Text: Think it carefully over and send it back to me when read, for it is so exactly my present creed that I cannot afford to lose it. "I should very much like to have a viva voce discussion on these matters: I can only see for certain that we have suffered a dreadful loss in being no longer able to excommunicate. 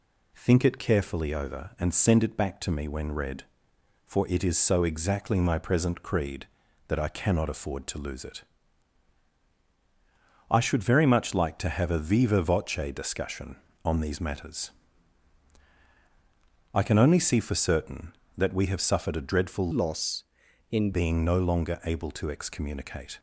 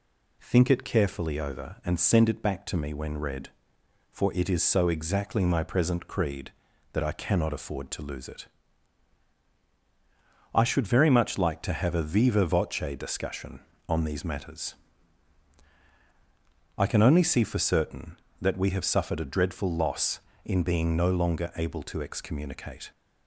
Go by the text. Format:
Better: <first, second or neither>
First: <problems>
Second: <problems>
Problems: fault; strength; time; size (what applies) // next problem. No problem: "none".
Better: second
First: changes voice from "loss" to "in"; from 19.7 to 20.9 s; 1.2 s long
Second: none